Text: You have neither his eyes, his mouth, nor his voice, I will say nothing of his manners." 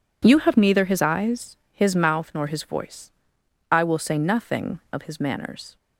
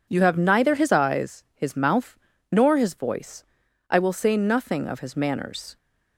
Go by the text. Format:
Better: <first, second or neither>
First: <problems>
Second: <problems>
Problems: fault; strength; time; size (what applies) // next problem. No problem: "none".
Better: neither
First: none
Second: none